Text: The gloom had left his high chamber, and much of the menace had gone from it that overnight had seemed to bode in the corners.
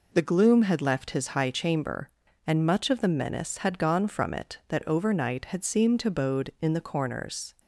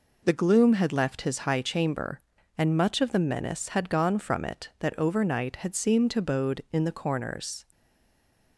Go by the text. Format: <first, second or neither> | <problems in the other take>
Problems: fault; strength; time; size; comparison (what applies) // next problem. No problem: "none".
first | stays silent after the last word; slight; from 7.7 s on; 0.8 s long